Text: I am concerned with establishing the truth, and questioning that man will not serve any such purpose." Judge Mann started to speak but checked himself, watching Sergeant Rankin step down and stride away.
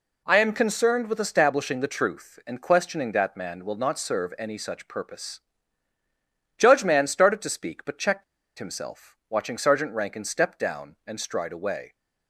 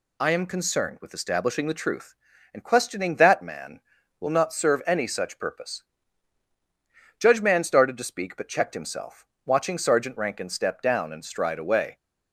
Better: second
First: pauses between "checked" and "himself"; slight; at 8.2 s; 0.35 s long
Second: none

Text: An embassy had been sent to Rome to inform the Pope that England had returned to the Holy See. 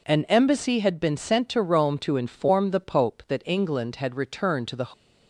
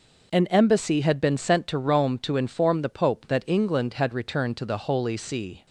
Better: second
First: stops before "Holy See"; at 4.9 s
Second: none

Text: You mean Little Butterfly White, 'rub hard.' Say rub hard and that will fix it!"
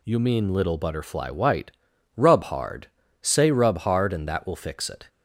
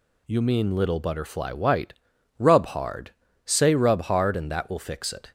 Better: neither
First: none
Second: none

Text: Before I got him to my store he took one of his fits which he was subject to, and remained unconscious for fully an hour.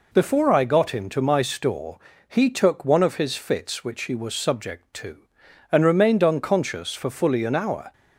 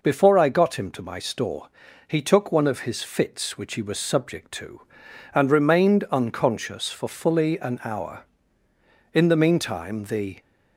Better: first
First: pauses between "store" and "he"; slight; at 1.9 s; 0.30 s long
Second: pauses between "store" and "he"; at 1.6 s; 0.40 s long // goes on to say "In the meantime the"; noticeable; from 9.1 s on; 1.2 s long

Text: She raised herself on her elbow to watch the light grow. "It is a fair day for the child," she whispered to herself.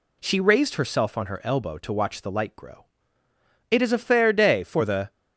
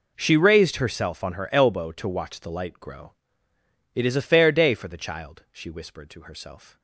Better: second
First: stops before "child she whispered to herself"; at 5.1 s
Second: none

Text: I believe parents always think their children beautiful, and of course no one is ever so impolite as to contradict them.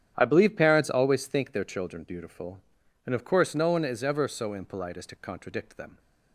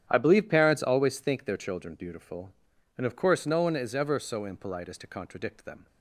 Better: neither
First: starts louder than the rest; strong; until 1.1 s; 9.5 dB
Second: starts louder than the rest; strong; until 1.1 s; 10 dB

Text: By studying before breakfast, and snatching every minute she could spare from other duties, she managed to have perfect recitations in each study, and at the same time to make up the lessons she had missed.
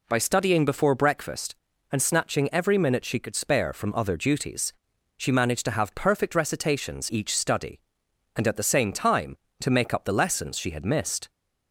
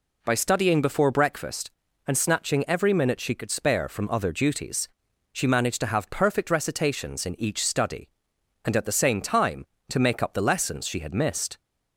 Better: second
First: skips "in"; at 7.1 s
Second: none

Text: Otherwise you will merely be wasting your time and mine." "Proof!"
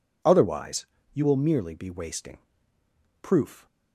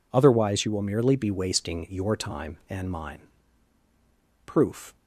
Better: second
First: pauses between "Otherwise" and "you"; slight; at 0.8 s; 0.26 s long // skips "your time and mine"; at 2.7 s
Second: none

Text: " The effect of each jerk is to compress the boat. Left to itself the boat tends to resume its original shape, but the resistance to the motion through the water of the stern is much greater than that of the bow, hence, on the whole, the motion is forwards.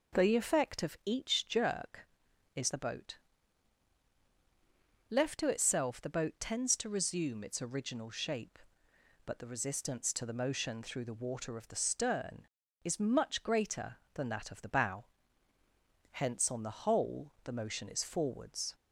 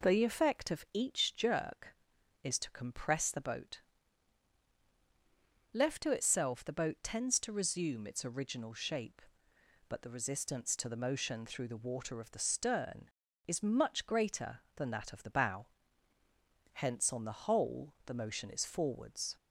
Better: second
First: skips "to compress"; at 2.6 s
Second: none

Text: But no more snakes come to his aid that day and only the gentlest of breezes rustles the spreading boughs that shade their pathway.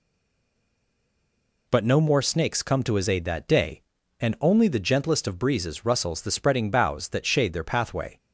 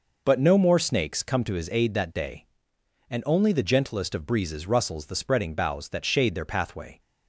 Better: second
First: stays silent before the first word; noticeable; until 1.6 s; 1.6 s long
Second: none

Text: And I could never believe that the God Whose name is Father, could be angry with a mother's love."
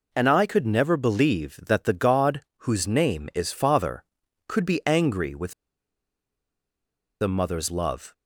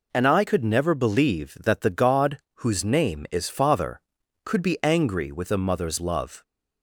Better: second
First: pauses between "God" and "Whose"; slight; at 2.4 s; 0.24 s long // pauses between "with" and "a"; strong; at 5.5 s; 1.6 s long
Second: pauses between "God" and "Whose"; slight; at 2.3 s; 0.24 s long

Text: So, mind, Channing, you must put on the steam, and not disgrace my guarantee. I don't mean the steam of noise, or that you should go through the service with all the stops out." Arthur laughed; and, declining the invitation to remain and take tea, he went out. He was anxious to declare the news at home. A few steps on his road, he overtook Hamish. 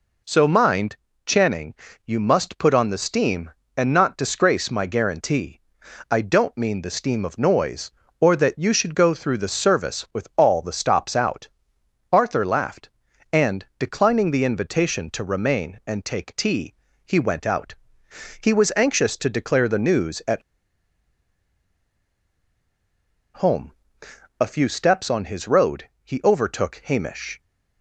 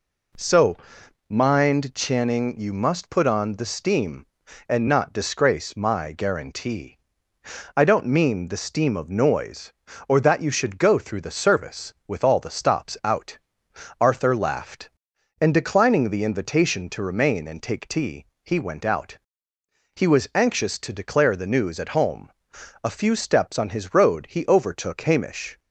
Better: second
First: pauses between "at" and "home"; strong; at 20.4 s; 2.9 s long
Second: none

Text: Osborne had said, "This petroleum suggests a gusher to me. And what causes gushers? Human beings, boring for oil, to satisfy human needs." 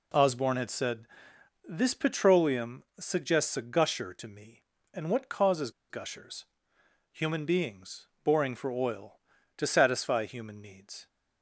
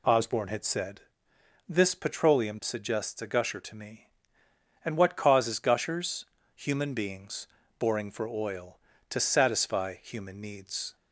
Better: second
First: pauses between "causes" and "gushers"; slight; at 5.7 s; 0.19 s long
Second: none

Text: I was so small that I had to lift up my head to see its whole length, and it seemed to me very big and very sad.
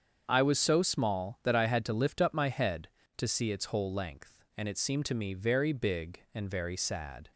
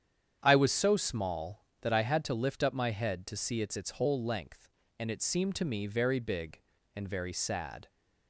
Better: first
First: starts louder than the rest; strong; until 1.2 s; 7.5 dB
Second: starts louder than the rest; strong; until 1.4 s; 8.5 dB // says "its" twice; at 3.7 s

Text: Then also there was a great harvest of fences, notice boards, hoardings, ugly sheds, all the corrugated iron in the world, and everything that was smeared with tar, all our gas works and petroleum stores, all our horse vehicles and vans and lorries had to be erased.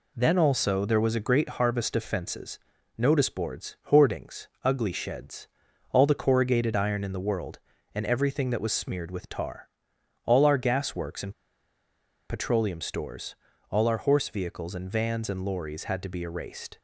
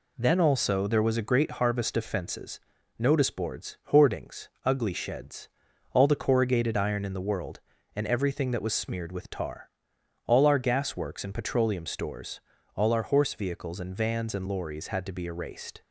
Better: second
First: pauses between "and" and "petroleum"; noticeable; at 11.3 s; 0.96 s long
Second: none

